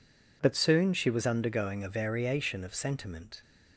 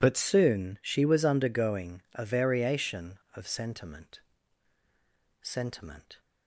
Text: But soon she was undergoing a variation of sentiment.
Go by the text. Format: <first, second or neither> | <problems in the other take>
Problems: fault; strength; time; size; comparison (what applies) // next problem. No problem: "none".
first | says "sentiment" twice; at 5.4 s